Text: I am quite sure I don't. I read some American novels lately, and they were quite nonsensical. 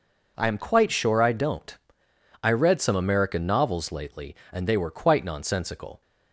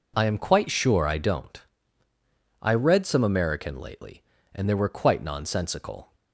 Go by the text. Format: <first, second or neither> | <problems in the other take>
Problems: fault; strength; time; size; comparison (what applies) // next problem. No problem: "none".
first | skips "novels"; at 3.8 s